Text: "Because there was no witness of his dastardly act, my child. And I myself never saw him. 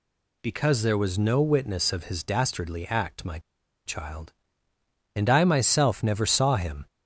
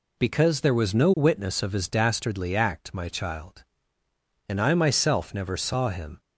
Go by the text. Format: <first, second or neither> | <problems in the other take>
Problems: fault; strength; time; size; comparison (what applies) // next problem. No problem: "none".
second | pauses between "my" and "child"; noticeable; at 3.3 s; 0.46 s long